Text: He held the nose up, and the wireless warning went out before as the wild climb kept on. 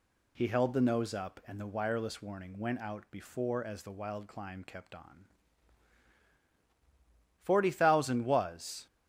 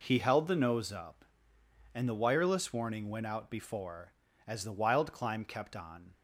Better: second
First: goes on to say "Forty thousand was"; from 7.4 s on; 1.4 s long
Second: none

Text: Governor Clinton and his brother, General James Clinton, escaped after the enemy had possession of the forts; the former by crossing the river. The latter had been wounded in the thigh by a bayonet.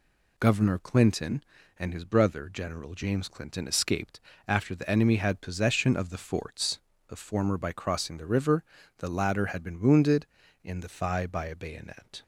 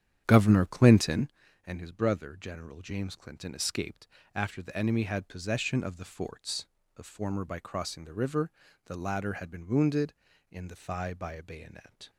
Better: first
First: pauses between "escaped" and "after"; slight; at 4.2 s; 0.26 s long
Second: starts louder than the rest; strong; until 1.3 s; 9 dB // pauses between "escaped" and "after"; slight; at 4.0 s; 0.26 s long

